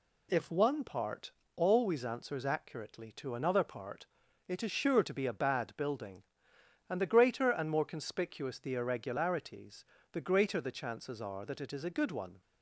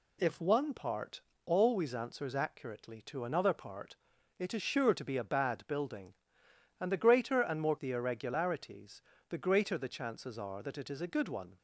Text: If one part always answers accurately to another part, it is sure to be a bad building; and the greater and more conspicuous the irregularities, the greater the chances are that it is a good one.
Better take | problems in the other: first | pauses between "part" and "always"; slight; at 1.2 s; 0.24 s long; slight in the first // skips "conspicuous"; at 7.7 s

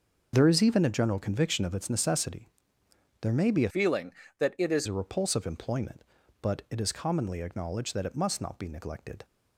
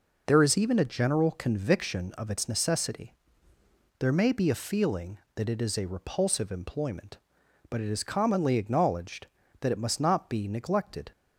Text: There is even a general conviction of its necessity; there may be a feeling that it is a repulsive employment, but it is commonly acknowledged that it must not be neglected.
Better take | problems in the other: second | changes voice from "feeling" to "is"; from 3.7 to 4.8 s; 1.1 s long

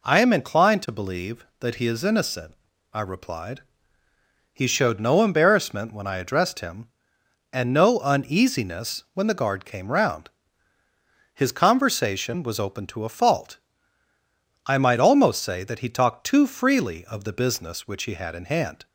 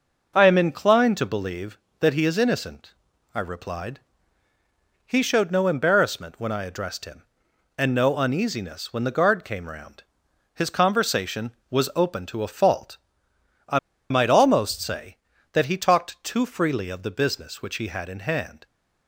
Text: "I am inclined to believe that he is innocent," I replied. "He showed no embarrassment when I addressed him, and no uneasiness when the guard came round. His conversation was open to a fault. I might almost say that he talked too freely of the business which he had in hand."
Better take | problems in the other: first | pauses between "I" and "might"; slight; at 13.7 s; 0.31 s long

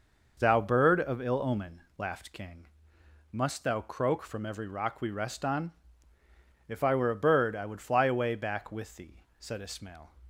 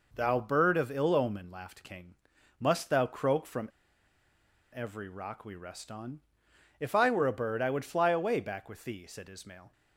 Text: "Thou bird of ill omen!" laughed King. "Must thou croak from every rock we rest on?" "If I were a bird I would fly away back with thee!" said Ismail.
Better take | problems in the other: first | pauses between "from" and "every"; at 3.6 s; 1.0 s long

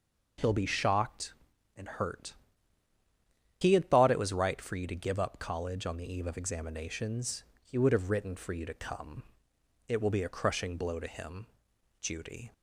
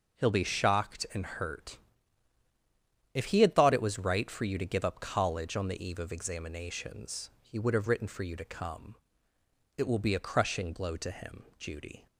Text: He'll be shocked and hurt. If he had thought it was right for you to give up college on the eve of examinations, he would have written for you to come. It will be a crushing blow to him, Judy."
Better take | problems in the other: second | skips "If"; at 2.9 s

